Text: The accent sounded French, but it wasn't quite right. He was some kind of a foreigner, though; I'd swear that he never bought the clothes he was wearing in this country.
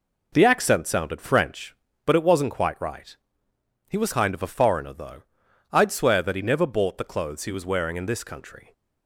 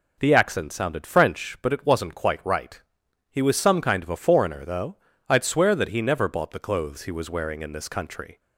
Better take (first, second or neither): second